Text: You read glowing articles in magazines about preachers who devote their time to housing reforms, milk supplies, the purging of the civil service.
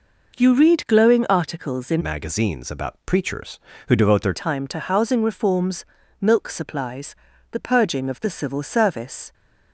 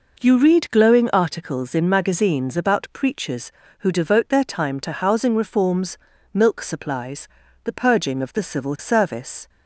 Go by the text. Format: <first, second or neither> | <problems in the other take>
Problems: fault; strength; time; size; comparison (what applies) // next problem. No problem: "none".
second | changes voice from "magazines" to "their"; from 2.0 to 4.3 s; 2.3 s long